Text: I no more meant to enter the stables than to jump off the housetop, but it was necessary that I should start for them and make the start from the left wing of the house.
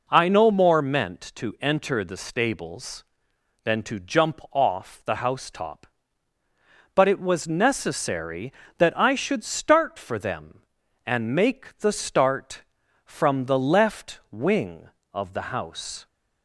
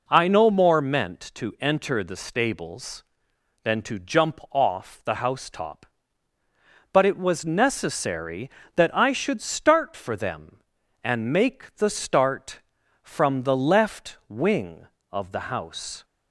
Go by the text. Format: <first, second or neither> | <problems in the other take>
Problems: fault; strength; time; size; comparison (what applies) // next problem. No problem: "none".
neither | none